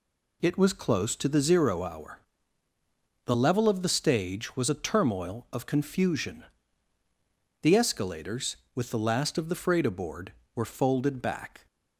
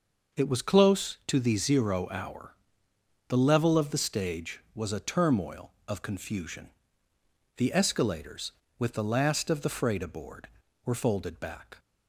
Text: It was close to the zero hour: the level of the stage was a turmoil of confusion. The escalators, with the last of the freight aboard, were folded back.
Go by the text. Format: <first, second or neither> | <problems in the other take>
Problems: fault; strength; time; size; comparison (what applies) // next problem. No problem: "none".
neither | none